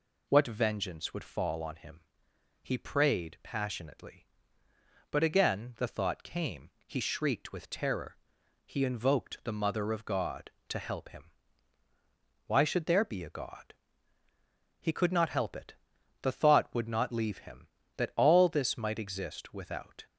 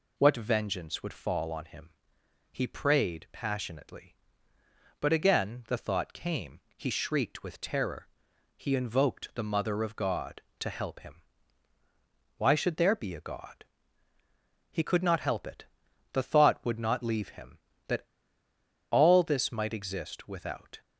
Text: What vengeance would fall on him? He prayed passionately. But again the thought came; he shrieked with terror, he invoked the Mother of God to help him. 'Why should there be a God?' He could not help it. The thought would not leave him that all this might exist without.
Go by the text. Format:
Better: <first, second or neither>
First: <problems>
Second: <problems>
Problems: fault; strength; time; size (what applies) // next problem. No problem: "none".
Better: first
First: none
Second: pauses between "that" and "all"; noticeable; at 18.0 s; 0.87 s long